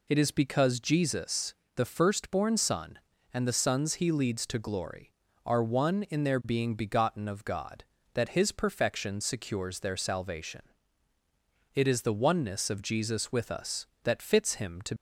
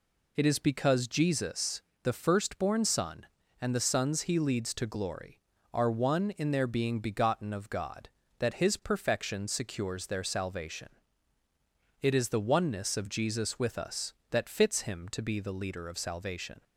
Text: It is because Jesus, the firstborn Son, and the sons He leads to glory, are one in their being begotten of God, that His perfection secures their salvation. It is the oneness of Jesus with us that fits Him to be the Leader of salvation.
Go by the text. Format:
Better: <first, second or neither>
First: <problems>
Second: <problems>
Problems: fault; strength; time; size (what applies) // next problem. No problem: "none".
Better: second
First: stops before "be the Leader of salvation"; at 14.9 s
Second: none